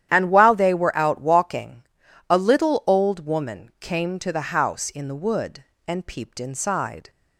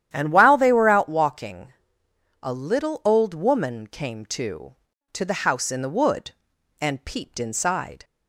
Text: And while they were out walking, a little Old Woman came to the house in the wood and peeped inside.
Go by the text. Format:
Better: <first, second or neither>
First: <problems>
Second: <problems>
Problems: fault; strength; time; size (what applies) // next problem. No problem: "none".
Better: first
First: starts louder than the rest; strong; until 1.1 s; 11 dB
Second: starts louder than the rest; strong; until 1.1 s; 10.5 dB // says "to" twice; at 5.1 s